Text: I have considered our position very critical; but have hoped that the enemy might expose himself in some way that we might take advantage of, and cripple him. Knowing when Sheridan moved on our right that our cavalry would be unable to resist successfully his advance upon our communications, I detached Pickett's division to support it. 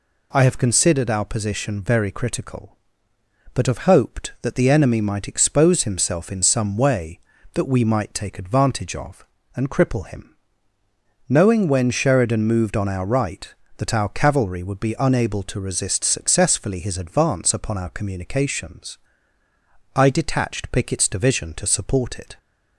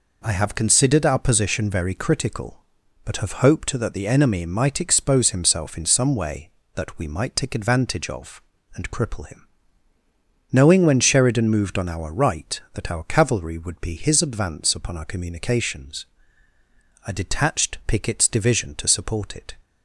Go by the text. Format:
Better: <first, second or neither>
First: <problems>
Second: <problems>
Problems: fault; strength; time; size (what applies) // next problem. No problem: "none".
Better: first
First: none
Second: skips "unable to resist successfully"; at 13.9 s